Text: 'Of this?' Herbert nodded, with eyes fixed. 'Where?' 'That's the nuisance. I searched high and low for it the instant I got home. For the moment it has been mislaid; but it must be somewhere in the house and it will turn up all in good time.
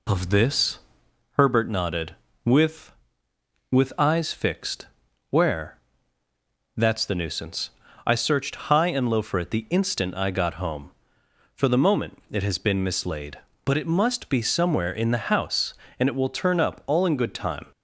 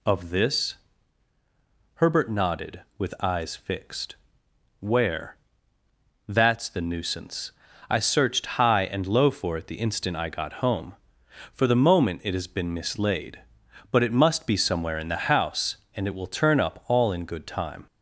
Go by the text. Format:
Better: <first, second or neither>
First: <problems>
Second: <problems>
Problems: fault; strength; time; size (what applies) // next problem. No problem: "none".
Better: second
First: says "with" twice; at 3.6 s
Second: none